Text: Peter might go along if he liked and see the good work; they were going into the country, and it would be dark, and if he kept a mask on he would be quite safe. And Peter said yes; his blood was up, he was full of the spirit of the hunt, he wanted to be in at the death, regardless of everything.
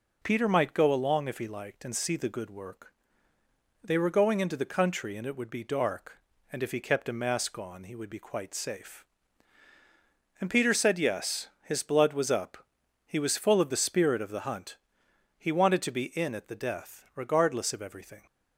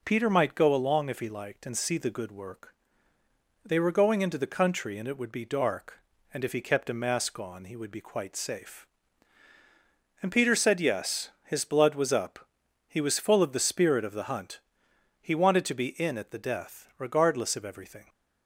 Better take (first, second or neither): neither